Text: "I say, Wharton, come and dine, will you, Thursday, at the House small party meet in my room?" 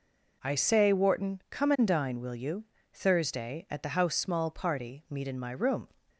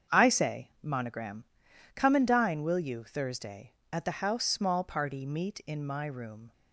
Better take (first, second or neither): first